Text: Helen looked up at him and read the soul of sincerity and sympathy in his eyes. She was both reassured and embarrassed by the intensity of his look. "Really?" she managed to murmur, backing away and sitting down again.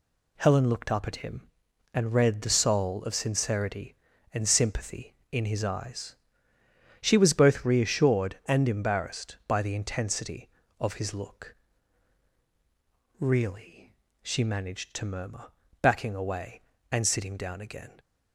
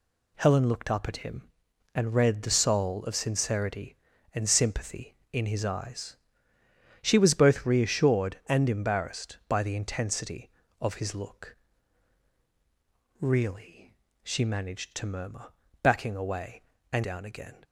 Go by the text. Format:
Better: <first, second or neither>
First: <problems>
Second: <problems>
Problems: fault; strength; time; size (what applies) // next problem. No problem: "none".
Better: first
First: none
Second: skips "sitting"; at 17.0 s